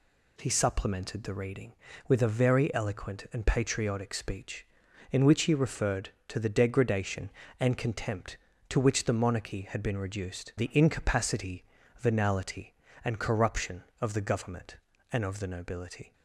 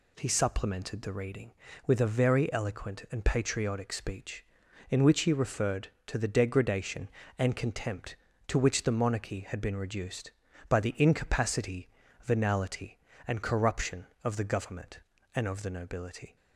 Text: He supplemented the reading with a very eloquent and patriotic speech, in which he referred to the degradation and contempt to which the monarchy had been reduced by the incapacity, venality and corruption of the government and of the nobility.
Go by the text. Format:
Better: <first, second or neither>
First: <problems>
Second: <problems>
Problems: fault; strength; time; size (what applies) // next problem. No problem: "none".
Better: second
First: skips "by"; at 10.5 s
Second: none